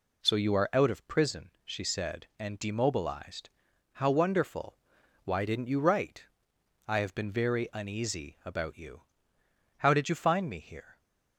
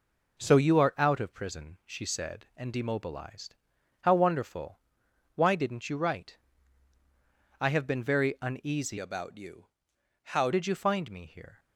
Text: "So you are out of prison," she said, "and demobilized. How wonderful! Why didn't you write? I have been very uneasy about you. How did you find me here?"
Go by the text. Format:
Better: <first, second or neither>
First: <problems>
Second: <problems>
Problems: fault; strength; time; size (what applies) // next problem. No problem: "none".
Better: first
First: none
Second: changes voice from "about" to "How"; from 8.9 to 10.5 s; 1.6 s long